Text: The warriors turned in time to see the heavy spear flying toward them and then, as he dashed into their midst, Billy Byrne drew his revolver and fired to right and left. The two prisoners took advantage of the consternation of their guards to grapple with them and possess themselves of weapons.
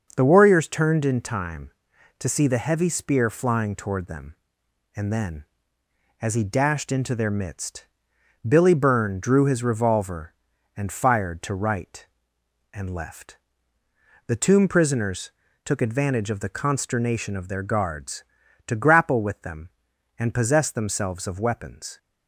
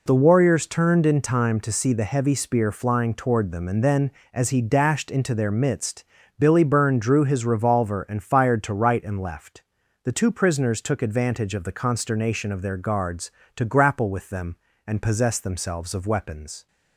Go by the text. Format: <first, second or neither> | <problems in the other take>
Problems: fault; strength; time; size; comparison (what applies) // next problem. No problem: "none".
second | says "tomb" for "two"; at 14.3 s // pauses between "prisoners" and "took"; slight; at 15.3 s; 0.32 s long